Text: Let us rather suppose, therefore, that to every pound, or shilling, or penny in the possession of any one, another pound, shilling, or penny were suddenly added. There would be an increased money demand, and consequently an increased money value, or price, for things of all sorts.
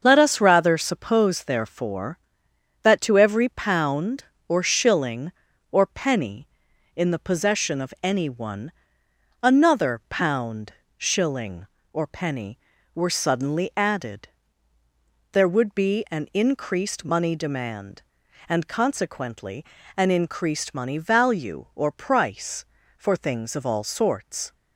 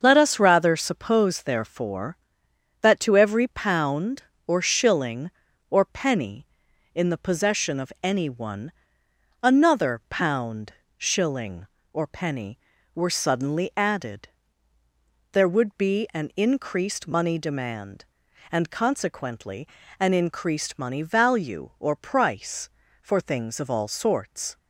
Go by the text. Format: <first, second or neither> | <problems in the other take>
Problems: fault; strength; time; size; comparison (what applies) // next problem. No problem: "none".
neither | starts louder than the rest; the same in both // pauses between "consequently" and "an"; slight; the same in both